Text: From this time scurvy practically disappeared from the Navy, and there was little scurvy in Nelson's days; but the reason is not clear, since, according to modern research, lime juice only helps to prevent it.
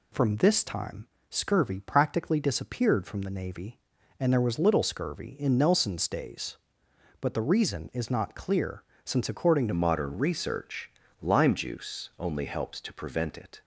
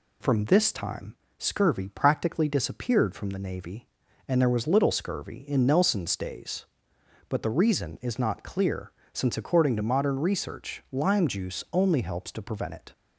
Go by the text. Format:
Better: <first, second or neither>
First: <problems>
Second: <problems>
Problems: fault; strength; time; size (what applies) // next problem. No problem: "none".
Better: second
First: pauses between "time" and "scurvy"; slight; at 1.0 s; 0.24 s long // changes voice at "modern"; from 9.7 s on; 3.9 s long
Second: pauses between "time" and "scurvy"; slight; at 1.1 s; 0.24 s long